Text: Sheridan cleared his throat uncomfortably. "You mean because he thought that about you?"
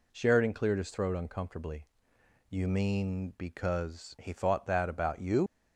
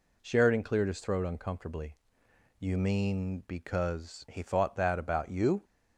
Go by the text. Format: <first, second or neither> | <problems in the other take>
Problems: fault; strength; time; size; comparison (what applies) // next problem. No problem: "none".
second | leaves "you" unfinished; at 5.4 s; 75 ms